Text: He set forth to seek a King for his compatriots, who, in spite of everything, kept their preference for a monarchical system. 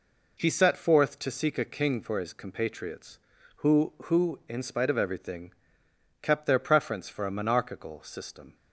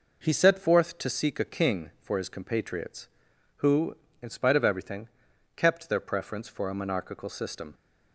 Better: second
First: says "who" twice; at 4.0 s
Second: none

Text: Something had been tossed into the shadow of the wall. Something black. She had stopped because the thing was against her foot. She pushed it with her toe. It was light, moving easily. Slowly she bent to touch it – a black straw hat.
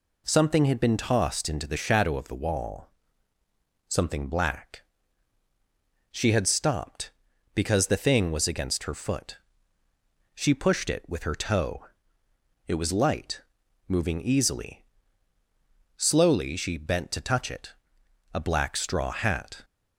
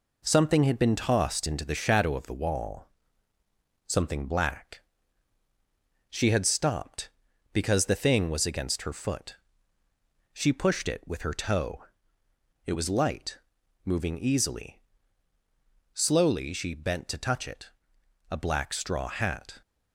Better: first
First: none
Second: gets quieter; noticeable; throughout; 5 dB

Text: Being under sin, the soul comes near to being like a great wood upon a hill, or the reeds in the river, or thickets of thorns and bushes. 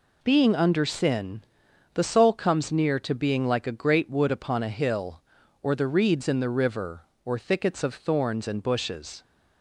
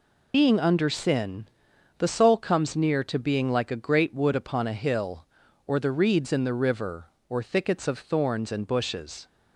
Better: first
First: none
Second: loses the start of "Being"; at 0.3 s; 75 ms

